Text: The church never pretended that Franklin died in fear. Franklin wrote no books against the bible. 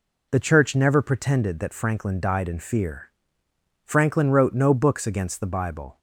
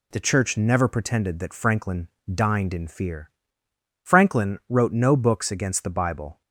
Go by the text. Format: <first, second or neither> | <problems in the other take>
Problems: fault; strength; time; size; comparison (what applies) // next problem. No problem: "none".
first | says "dined" for "died"; at 2.3 s